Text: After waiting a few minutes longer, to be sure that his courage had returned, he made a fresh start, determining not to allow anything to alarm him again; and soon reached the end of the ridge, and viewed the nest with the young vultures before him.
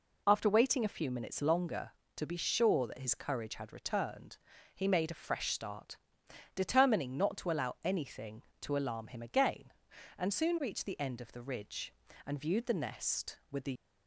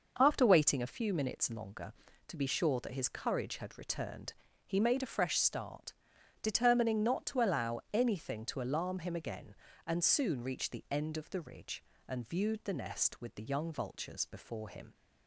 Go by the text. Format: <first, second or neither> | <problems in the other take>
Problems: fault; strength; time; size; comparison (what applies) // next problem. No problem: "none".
second | stops before "young vultures before him"; at 13.7 s